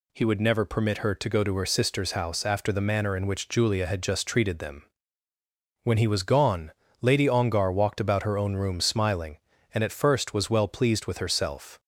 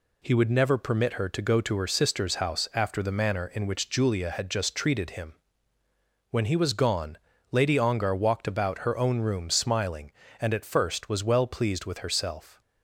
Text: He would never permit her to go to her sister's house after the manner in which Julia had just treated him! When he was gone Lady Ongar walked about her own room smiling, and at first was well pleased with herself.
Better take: second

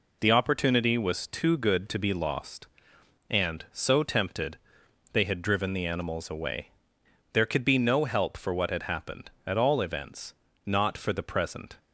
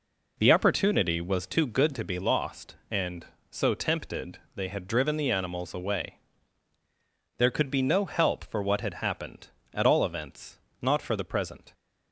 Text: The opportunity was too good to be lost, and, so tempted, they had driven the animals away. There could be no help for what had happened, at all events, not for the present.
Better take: neither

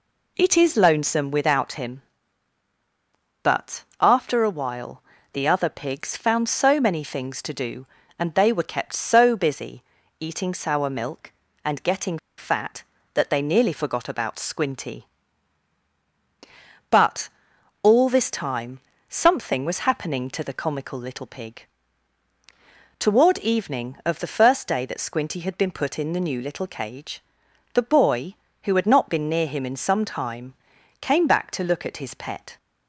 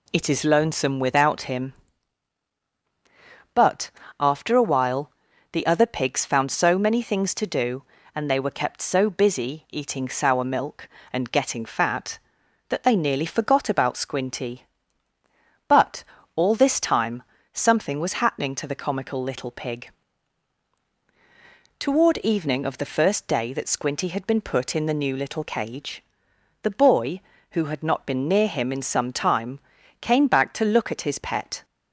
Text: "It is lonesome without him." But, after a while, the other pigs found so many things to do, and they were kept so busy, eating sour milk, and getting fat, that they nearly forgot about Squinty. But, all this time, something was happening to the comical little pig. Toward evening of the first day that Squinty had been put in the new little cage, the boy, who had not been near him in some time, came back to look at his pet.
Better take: second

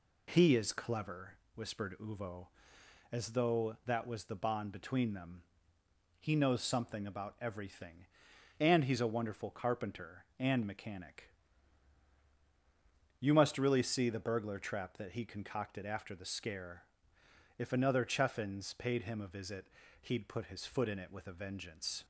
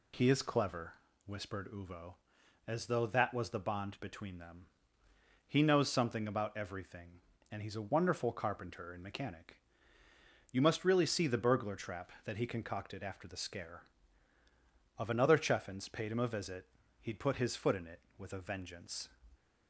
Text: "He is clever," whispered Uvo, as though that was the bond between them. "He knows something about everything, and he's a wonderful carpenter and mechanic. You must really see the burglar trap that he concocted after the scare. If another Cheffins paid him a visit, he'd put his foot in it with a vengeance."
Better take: first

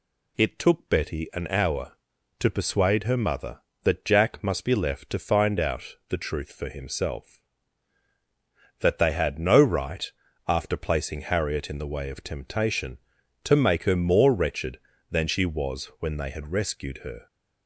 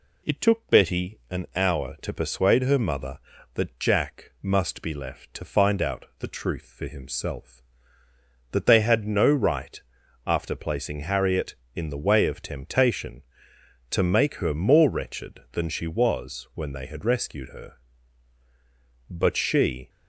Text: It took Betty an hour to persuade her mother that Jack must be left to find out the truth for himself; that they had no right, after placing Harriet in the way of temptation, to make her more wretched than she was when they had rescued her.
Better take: first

